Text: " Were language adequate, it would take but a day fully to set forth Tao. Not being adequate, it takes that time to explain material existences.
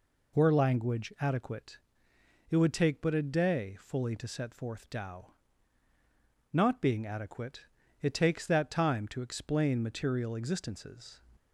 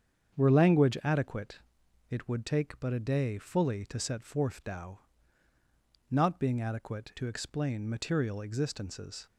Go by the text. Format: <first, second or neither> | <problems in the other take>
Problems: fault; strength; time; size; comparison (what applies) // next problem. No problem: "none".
first | starts louder than the rest; strong; until 1.4 s; 7.5 dB // skips "it takes that time"; at 7.1 s